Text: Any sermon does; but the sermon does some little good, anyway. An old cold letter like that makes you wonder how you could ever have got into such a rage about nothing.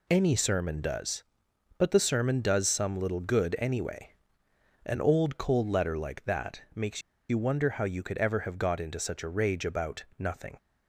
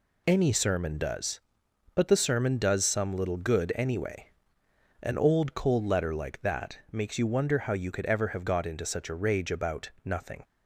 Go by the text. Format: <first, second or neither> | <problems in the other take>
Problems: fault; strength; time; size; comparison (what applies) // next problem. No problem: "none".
second | pauses between "makes" and "you"; slight; at 7.0 s; 0.28 s long